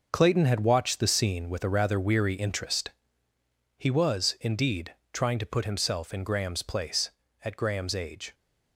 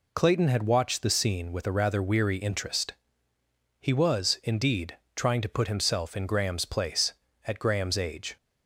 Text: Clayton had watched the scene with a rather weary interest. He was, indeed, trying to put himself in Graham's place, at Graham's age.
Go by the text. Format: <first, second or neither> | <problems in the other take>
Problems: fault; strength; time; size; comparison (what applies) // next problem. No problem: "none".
second | gets quieter; strong; throughout; 8.5 dB